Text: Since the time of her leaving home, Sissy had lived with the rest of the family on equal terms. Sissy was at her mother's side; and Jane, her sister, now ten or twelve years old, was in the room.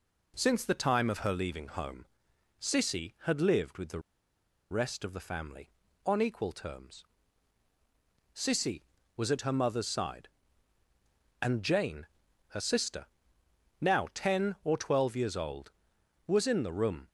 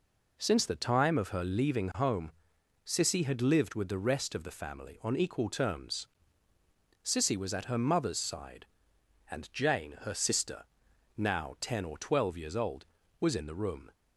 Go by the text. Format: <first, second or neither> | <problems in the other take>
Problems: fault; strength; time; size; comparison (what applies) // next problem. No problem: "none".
second | pauses between "the" and "rest"; noticeable; at 4.0 s; 0.69 s long